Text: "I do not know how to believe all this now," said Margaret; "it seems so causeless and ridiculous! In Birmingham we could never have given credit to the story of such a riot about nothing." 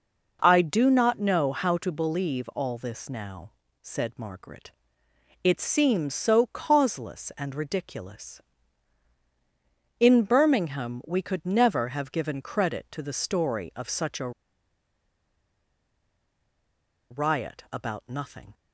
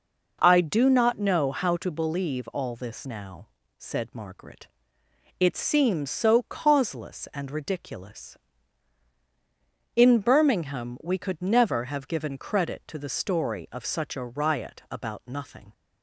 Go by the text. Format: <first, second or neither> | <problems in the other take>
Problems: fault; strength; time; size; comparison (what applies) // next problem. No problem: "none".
second | pauses between "a" and "riot"; strong; at 14.3 s; 2.8 s long